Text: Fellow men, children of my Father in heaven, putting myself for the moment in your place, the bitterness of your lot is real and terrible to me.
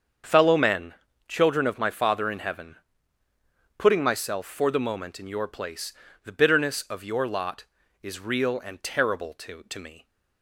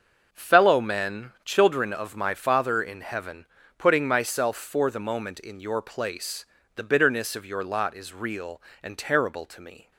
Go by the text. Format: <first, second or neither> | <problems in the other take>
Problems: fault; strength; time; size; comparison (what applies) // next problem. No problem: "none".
second | starts louder than the rest; until 1.5 s; 7 dB; noticeable in the second // says "to" twice; at 9.6 s